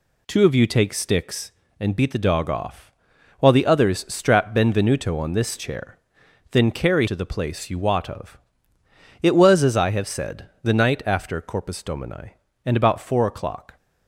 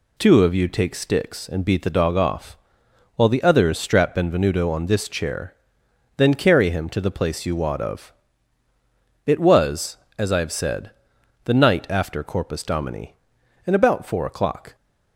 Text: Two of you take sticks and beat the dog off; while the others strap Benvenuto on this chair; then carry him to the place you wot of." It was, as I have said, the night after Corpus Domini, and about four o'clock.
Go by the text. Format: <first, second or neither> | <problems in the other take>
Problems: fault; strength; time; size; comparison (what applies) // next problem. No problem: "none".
second | skips "him"; at 7.0 s